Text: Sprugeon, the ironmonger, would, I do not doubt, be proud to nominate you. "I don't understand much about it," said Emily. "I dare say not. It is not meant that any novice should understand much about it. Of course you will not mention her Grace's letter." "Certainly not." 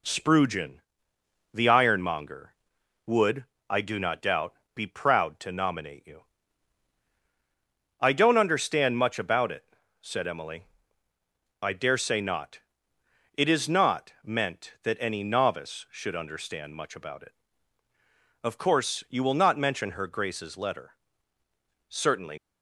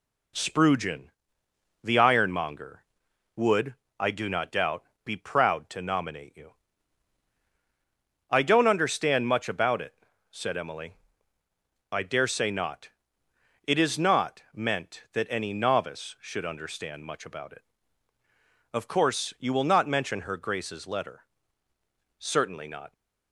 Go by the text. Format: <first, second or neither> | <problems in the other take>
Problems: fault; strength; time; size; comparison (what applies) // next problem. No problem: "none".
second | stops before "not"; at 22.3 s